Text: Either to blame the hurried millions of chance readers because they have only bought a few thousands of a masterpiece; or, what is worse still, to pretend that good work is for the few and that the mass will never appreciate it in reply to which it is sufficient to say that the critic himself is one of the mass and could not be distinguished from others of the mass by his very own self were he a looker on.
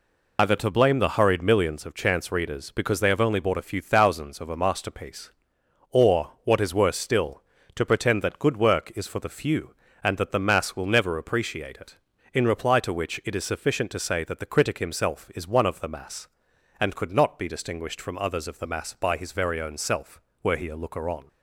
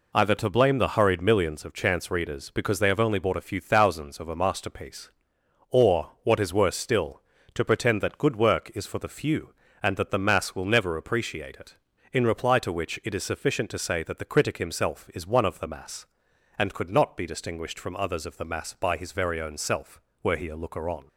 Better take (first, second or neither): second